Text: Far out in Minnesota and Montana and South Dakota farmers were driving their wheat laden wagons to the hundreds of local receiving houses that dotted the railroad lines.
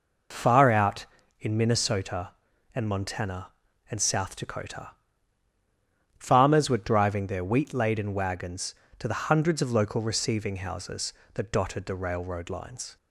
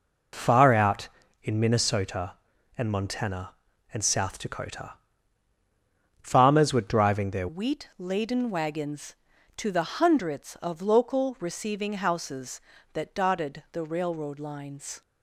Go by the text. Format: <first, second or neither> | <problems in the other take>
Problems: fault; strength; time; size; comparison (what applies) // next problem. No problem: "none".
first | pauses between "Dakota" and "farmers"; strong; at 4.9 s; 1.2 s long; strong in the first // changes voice at "wheat"; from 7.4 s on; 7.6 s long